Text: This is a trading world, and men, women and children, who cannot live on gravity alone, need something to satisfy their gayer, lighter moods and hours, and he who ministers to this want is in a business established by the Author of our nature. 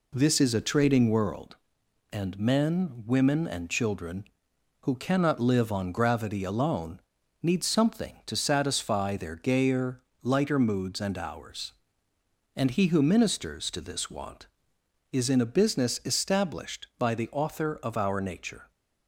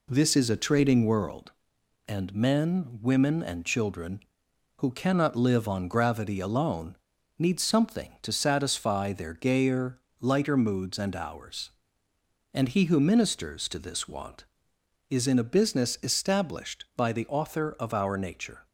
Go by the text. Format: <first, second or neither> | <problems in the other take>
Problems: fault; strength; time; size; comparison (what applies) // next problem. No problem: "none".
neither | none